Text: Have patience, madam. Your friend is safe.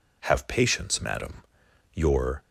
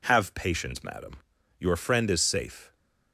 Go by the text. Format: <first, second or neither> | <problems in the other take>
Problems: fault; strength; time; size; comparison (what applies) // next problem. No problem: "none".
second | stops before "friend is safe"; at 2.4 s